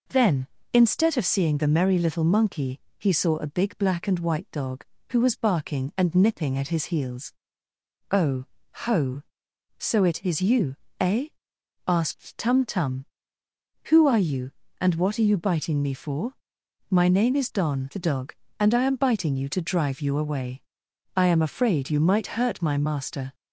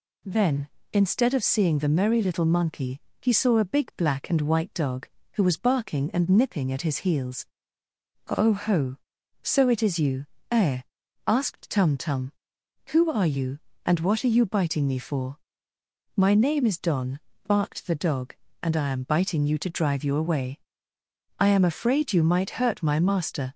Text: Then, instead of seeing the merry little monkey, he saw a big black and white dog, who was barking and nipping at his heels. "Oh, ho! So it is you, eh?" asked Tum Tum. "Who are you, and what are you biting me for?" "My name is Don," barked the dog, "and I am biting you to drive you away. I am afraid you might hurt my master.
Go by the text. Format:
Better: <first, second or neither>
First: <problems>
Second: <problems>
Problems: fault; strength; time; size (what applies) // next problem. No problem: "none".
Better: second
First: skips "barked"; at 17.9 s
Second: none